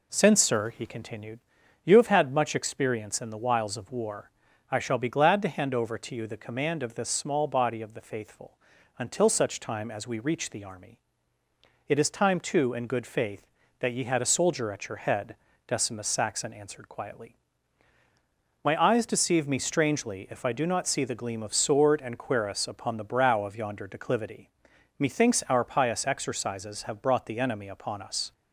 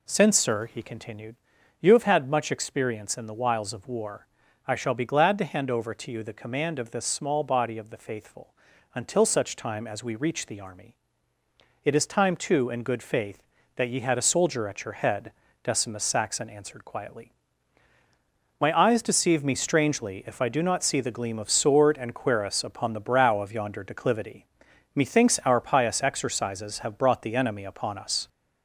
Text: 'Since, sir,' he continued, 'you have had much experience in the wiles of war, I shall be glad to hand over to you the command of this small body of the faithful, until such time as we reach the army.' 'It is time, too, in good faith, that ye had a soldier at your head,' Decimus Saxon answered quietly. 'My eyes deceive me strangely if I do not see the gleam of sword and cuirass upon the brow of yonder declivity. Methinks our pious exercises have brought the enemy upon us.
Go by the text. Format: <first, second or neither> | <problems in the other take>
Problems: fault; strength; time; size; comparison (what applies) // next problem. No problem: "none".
first | gets louder; throughout; 3.5 dB